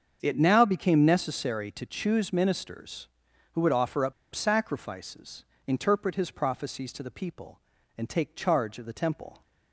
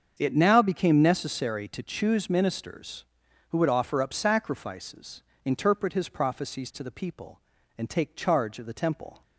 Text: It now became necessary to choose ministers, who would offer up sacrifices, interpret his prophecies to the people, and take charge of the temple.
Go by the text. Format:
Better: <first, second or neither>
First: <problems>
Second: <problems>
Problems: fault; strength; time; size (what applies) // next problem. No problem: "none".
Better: second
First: starts louder than the rest; until 1.2 s; 7 dB // pauses between "up" and "sacrifices"; slight; at 4.1 s; 0.20 s long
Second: starts louder than the rest; until 1.1 s; 7 dB